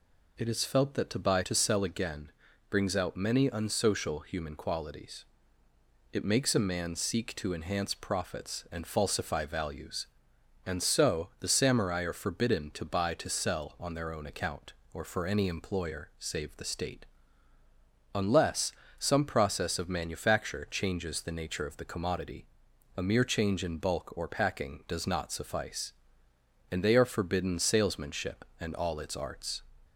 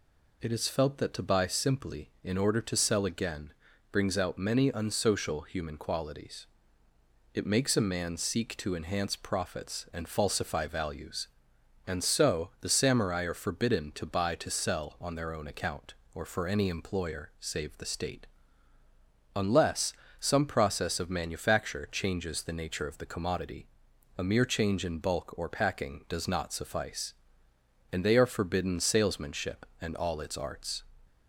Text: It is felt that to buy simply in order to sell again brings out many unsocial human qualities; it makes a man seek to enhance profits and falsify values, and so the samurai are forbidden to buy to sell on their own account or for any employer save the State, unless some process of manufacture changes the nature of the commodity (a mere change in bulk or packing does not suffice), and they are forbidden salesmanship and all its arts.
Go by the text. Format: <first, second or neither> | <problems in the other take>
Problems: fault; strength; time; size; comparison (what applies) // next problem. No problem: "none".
second | skips "simply in order"; at 1.4 s // pauses between "again" and "brings"; at 2.3 s; 0.40 s long; also in the second // pauses between "unless" and "some"; slight; at 18.7 s; 0.30 s long; slight in the second